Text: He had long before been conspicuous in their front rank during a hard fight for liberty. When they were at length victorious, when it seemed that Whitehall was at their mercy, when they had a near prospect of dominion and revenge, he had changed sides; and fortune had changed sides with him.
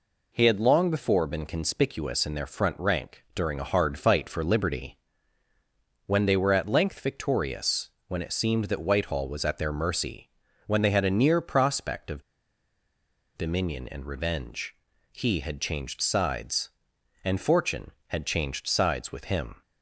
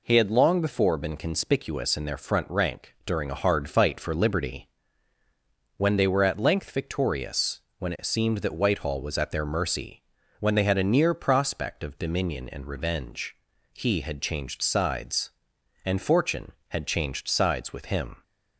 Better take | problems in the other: second | pauses between "of" and "dominion"; at 12.2 s; 1.1 s long

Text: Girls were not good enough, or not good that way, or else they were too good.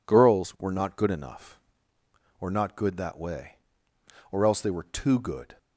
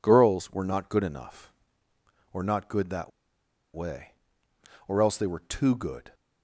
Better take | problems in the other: first | pauses between "that" and "way"; noticeable; at 3.1 s; 0.65 s long

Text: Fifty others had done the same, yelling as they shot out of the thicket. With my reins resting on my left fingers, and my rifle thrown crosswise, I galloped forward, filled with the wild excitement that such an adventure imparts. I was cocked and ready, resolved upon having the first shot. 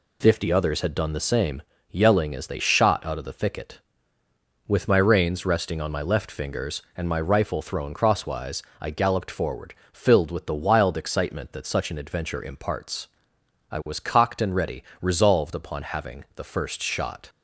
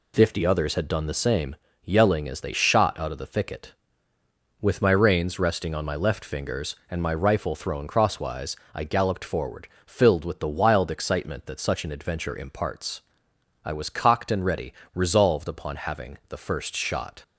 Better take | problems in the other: neither | none

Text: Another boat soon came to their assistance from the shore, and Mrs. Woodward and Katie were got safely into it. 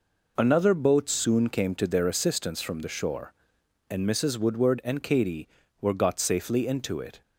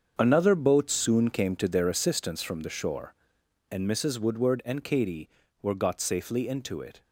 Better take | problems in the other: first | gets quieter; strong; throughout; 12 dB

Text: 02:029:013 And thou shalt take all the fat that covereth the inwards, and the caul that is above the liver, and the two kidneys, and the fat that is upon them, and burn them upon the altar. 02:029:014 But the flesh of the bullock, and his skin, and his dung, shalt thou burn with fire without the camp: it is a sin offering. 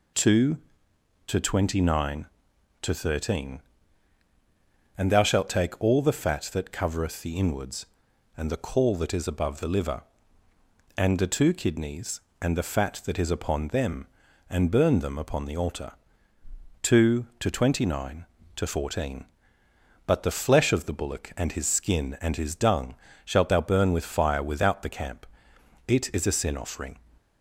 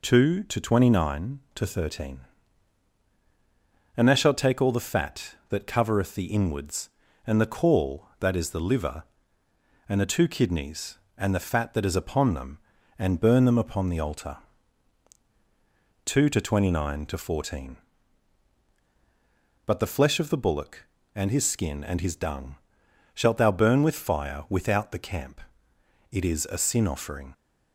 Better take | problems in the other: first | skips "above"; at 8.5 s

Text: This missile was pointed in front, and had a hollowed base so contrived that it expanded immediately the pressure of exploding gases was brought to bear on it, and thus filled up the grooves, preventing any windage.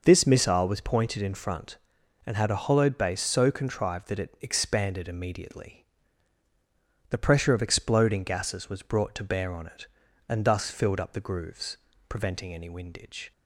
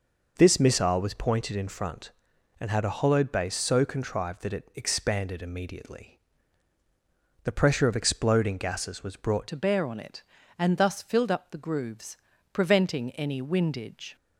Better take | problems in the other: first | pauses between "immediately" and "the"; at 6.1 s; 1.2 s long; also in the first // changes voice at "to"; from 9.4 s on; 4.7 s long

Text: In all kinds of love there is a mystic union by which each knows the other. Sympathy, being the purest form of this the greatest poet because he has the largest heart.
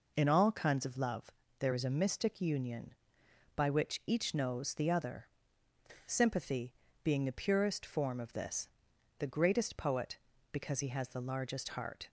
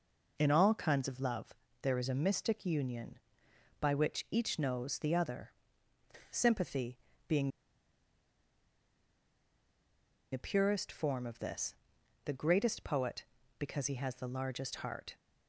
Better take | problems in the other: first | pauses between "love" and "there"; slight; at 1.5 s; 0.26 s long; slight in the first // pauses between "being" and "the"; strong; at 7.4 s; 2.8 s long // pauses between "this" and "the"; noticeable; at 11.7 s; 0.52 s long; noticeable in the first

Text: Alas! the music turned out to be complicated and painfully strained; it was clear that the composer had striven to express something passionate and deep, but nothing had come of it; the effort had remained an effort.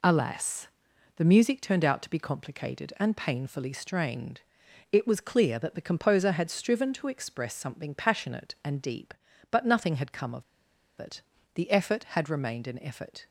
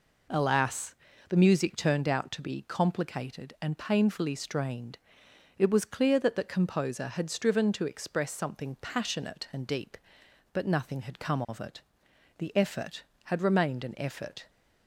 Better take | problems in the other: second | pauses between "of" and "it"; noticeable; at 10.4 s; 0.54 s long

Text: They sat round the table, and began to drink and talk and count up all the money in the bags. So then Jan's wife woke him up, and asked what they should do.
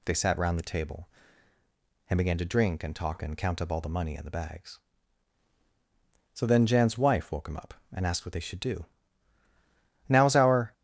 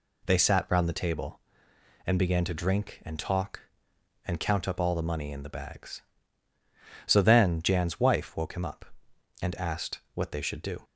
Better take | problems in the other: second | goes on to say "Now's our"; noticeable; from 10.0 s on; 0.64 s long

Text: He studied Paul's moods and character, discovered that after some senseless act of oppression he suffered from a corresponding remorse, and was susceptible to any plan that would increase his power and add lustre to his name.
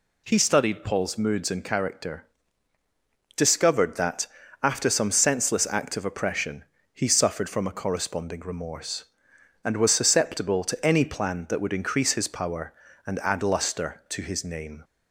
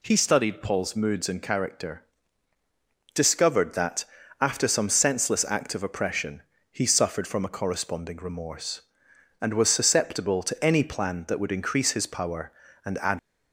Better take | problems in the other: first | pauses between "that" and "after"; slight; at 4.0 s; 0.36 s long; slight in the first // pauses between "oppression" and "he"; slight; at 6.4 s; 0.30 s long; slight in the first // stops before "lustre to his name"; at 13.1 s

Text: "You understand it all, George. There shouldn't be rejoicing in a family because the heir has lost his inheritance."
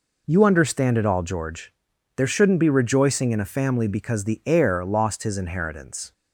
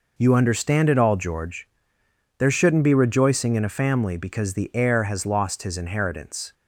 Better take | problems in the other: second | skips "has"; at 4.8 s

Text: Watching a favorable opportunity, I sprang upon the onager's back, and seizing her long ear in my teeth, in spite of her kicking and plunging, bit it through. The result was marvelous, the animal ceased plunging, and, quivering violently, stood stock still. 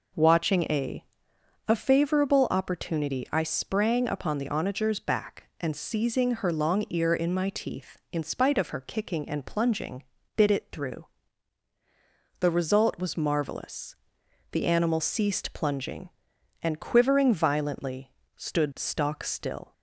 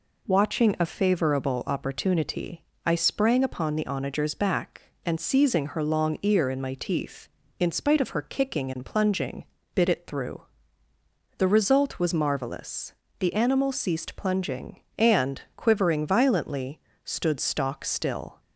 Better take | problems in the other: second | says "a" twice; at 1.6 s

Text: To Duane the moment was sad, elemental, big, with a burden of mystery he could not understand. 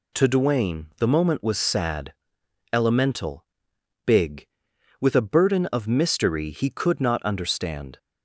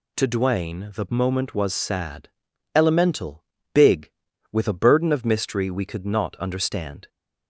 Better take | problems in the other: first | says "we" for "he"; at 5.7 s

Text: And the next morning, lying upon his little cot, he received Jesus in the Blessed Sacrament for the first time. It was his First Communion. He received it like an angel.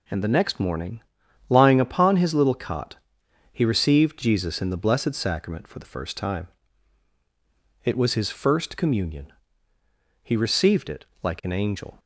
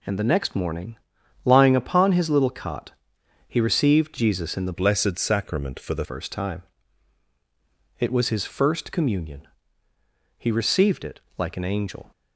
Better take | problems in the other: first | changes voice from "Blessed" to "the"; from 4.7 to 6.0 s; 1.3 s long // pauses between "it" and "like"; slight; at 11.2 s; 0.16 s long; slight in the first

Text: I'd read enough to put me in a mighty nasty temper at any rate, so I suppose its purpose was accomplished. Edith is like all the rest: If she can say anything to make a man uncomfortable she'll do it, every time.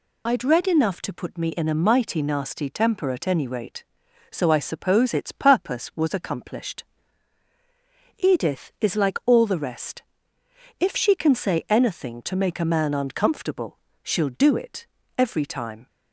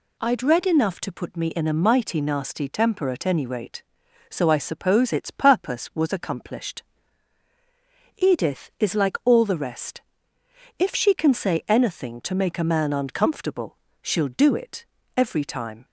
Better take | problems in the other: second | loses the start of "I'd"; at 0.2 s; 50 ms // pauses between "uncomfortable" and "she'll"; slight; at 13.7 s; 0.26 s long; slight in the second

